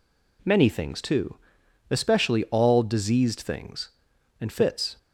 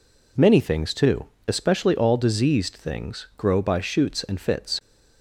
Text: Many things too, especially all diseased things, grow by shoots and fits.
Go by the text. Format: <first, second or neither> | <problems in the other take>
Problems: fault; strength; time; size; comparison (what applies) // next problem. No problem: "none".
second | skips "grow by shoots"; at 4.1 s